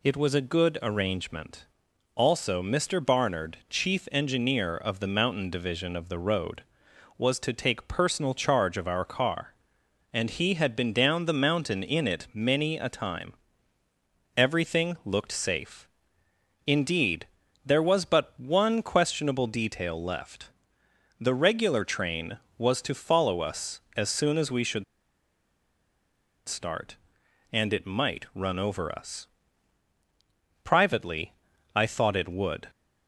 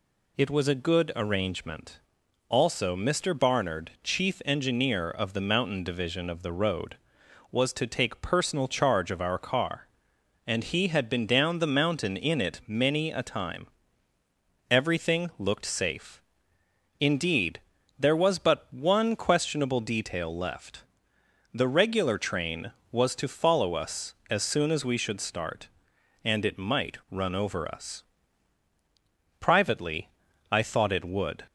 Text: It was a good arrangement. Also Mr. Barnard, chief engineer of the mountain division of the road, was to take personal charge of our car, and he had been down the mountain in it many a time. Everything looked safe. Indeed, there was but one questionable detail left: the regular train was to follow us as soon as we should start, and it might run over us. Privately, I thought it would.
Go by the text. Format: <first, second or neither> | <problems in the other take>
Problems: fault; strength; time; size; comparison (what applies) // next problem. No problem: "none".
second | pauses between "should" and "start"; strong; at 24.8 s; 1.6 s long